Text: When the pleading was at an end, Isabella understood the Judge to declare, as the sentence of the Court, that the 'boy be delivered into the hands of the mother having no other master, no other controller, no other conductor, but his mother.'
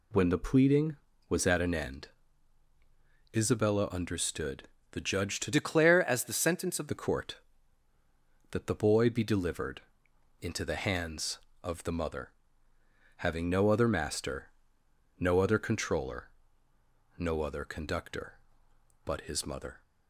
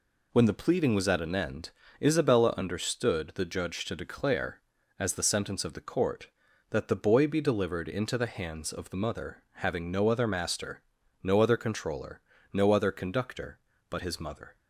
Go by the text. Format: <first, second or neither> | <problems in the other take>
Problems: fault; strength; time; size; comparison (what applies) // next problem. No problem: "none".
second | pauses between "understood" and "the"; slight; at 4.6 s; 0.22 s long // changes voice from "declare" to "of"; from 5.5 to 6.8 s; 1.3 s long // pauses between "delivered" and "into"; noticeable; at 9.8 s; 0.60 s long // pauses between "mother" and "having"; noticeable; at 12.3 s; 0.86 s long